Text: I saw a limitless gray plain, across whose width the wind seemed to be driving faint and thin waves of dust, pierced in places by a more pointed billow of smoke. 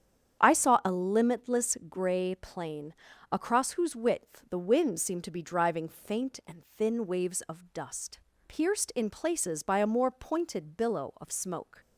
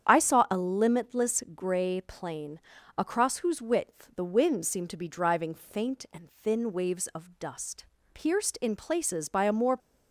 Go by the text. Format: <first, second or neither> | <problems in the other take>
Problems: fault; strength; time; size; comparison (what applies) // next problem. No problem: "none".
first | starts louder than the rest; strong; until 1.1 s; 8.5 dB; strong in the first // stops before "pointed billow of smoke"; at 9.7 s